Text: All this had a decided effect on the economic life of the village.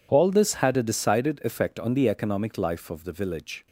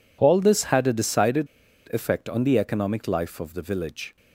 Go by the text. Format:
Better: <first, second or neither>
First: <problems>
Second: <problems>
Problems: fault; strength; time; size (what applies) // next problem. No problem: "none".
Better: first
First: none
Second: pauses between "decided" and "effect"; noticeable; at 1.4 s; 0.46 s long